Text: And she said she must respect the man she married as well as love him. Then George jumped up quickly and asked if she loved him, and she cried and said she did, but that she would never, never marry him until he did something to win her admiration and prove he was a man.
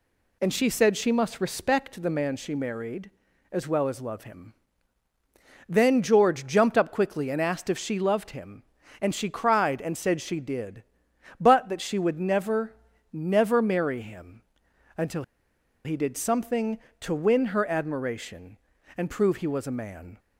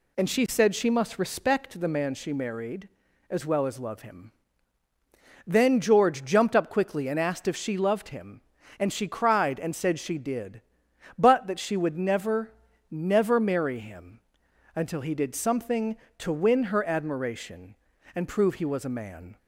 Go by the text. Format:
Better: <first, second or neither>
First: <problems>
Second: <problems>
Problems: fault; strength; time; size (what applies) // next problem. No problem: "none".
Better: second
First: pauses between "him" and "until"; noticeable; at 14.4 s; 0.54 s long // pauses between "until" and "he"; noticeable; at 15.2 s; 0.62 s long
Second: pauses between "him" and "until"; noticeable; at 14.2 s; 0.54 s long